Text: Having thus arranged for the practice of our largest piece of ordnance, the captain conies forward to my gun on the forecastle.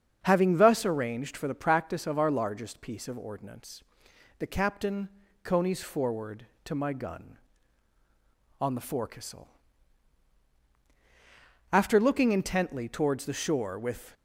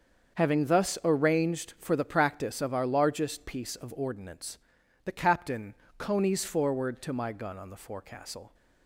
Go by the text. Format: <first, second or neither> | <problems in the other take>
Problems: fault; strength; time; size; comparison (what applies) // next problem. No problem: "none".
second | starts louder than the rest; until 1.2 s; 7 dB; also in the second // pauses between "captain" and "conies"; slight; at 5.0 s; 0.36 s long; slight in the second // goes on to say "After looking intently towards the shore with"; strong; from 11.7 s on; 2.4 s long